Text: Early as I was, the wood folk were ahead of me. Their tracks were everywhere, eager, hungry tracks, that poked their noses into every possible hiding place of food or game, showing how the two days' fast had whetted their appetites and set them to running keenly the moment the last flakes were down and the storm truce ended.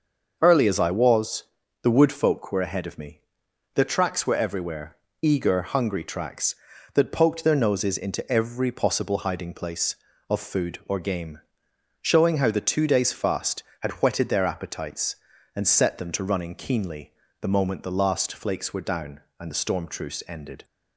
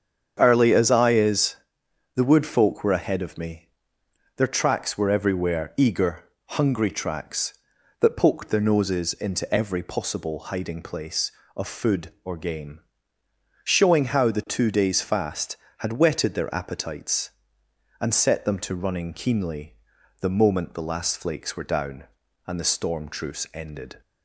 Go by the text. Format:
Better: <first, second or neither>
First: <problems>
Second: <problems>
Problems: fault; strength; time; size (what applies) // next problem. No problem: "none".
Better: first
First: starts louder than the rest; until 1.4 s; 6.5 dB // pauses between "keenly" and "the"; slight; at 17.1 s; 0.28 s long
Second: starts louder than the rest; strong; until 1.3 s; 7.5 dB // says "is" for "was"; at 1.1 s // pauses between "keenly" and "the"; noticeable; at 19.7 s; 0.46 s long